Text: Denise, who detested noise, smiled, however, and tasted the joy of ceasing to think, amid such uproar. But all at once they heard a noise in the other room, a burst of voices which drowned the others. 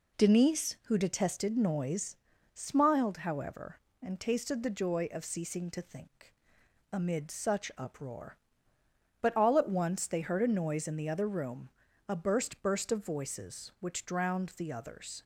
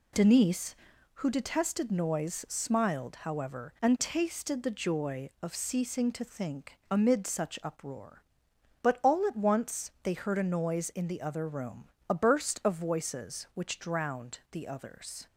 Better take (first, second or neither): second